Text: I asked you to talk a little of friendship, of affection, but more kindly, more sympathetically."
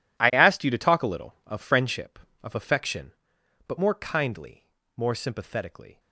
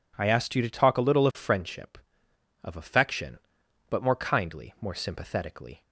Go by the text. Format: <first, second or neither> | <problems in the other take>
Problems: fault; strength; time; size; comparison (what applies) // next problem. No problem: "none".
second | gets quieter; strong; throughout; 16 dB